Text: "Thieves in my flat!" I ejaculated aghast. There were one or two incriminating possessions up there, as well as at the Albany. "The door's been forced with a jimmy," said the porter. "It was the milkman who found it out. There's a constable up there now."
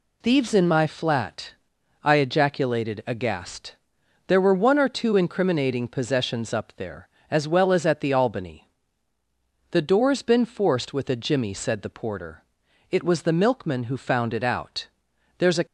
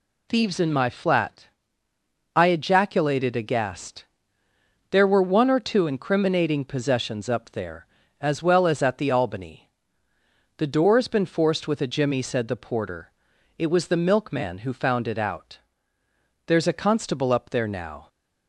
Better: second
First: stops before "constable up there now"; at 15.6 s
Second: none

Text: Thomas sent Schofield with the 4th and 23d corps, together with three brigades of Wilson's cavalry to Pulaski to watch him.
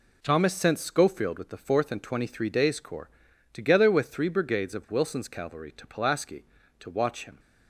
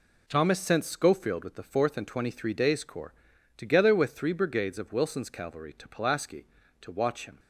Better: neither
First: none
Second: none

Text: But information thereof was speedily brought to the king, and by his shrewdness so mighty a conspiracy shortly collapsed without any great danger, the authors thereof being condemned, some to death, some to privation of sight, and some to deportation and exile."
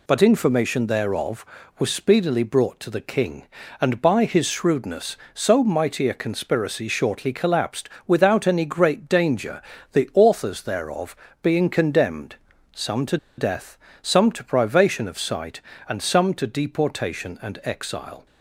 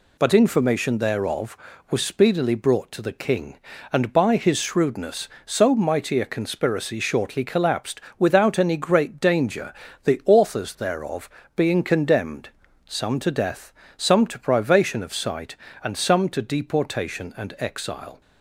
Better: second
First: pauses between "collapsed" and "without"; slight; at 7.8 s; 0.18 s long // pauses between "thereof" and "being"; slight; at 11.1 s; 0.26 s long // pauses between "to" and "death"; slight; at 13.1 s; 0.21 s long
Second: pauses between "collapsed" and "without"; slight; at 8.0 s; 0.18 s long // pauses between "thereof" and "being"; slight; at 11.3 s; 0.26 s long

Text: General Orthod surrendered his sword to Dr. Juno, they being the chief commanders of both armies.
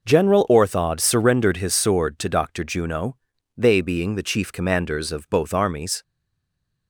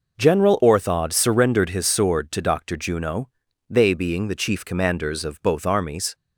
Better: second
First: stays silent after the last word; slight; from 6.0 s on; 0.8 s long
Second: none

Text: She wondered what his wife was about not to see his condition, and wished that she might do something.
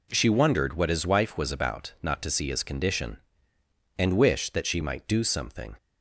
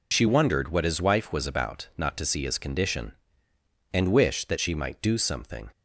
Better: first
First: none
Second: loses the start of "She"; at 0.1 s; 45 ms

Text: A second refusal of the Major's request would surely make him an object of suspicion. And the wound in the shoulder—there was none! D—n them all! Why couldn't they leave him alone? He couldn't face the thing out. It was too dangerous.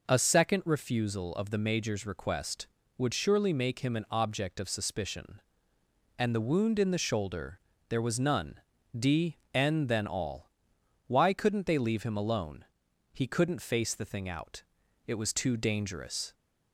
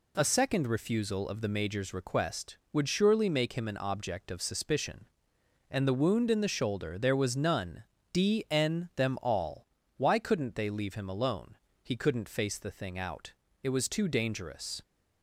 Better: second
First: says "then" for "them"; at 9.8 s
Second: none

